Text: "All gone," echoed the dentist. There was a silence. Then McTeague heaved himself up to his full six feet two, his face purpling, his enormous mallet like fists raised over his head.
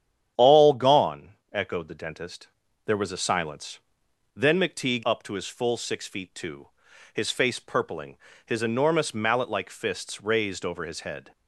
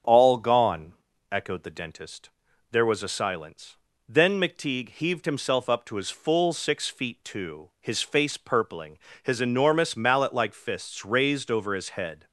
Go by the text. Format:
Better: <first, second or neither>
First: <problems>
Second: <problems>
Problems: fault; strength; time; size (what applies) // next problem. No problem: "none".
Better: second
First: starts louder than the rest; strong; until 1.5 s; 9.5 dB // skips "heaved himself"; at 5.0 s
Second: starts louder than the rest; until 1.4 s; 7 dB